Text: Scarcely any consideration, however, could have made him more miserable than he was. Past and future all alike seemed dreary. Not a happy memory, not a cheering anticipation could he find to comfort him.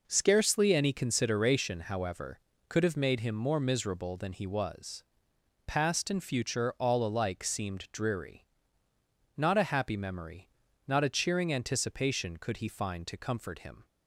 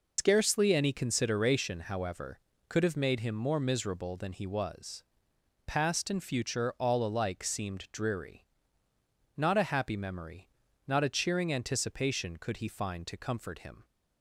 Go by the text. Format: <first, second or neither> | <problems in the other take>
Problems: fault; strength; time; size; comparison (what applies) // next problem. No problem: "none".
first | loses the start of "Scarcely"; at 0.1 s; 115 ms